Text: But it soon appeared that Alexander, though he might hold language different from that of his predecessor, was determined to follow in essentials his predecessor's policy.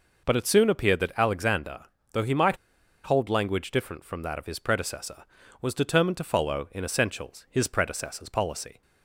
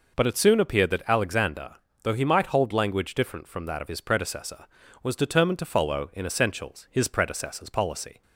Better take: second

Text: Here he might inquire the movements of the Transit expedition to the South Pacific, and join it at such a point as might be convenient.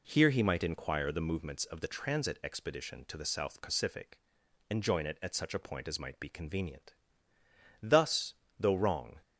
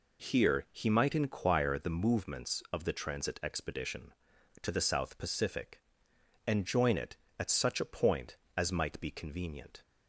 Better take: second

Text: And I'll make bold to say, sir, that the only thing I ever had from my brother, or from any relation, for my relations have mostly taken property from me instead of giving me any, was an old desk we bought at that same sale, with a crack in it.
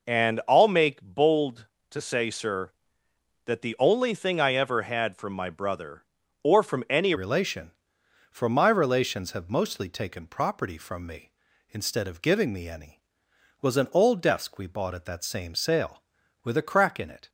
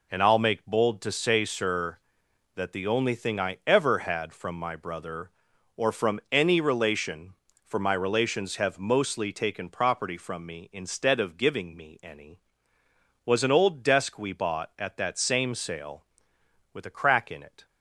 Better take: second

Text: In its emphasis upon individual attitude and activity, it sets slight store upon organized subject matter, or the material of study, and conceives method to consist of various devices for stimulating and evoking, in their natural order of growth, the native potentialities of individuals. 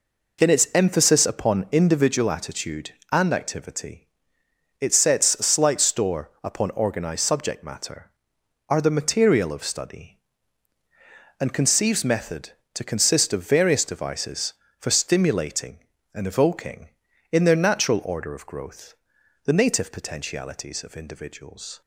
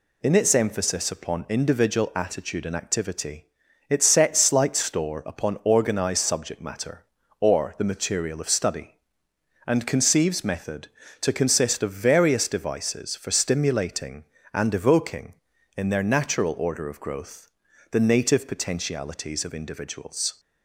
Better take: second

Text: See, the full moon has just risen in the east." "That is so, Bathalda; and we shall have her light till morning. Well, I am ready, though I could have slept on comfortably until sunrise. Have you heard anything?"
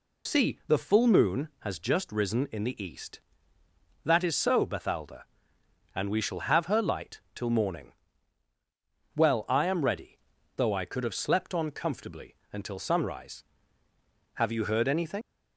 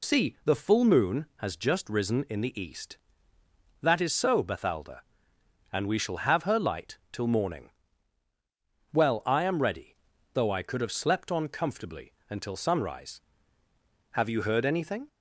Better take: second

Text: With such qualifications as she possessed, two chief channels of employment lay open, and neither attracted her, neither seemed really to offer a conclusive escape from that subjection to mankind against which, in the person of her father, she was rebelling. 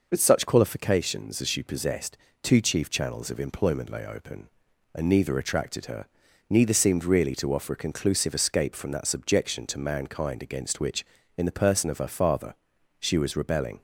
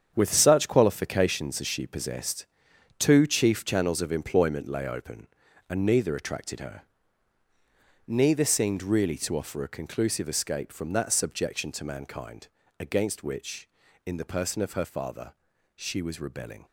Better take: first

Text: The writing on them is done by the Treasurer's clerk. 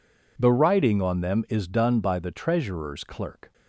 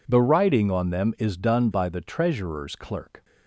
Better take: neither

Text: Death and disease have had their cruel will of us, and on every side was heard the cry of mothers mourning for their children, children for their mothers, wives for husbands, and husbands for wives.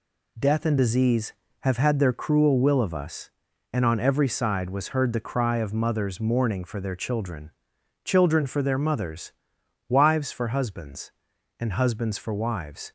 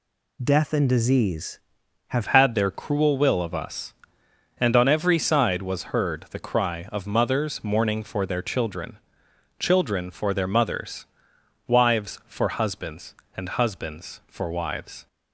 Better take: first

